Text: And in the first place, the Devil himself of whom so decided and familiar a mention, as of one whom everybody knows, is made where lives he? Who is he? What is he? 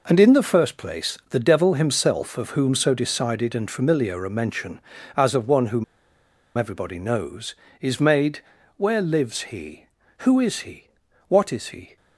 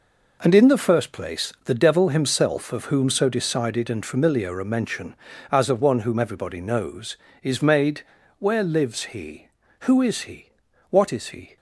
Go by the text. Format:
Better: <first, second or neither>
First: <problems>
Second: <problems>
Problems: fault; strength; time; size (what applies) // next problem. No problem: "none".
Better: second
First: pauses between "whom" and "everybody"; noticeable; at 5.8 s; 0.73 s long // pauses between "made" and "where"; slight; at 8.4 s; 0.36 s long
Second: pauses between "made" and "where"; slight; at 8.0 s; 0.36 s long